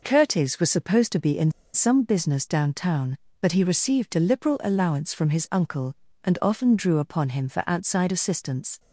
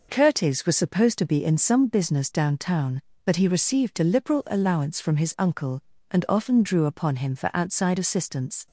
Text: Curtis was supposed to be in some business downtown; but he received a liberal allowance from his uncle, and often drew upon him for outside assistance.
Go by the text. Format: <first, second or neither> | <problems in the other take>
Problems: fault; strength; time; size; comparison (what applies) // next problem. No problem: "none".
second | pauses between "in" and "some"; slight; at 1.4 s; 0.24 s long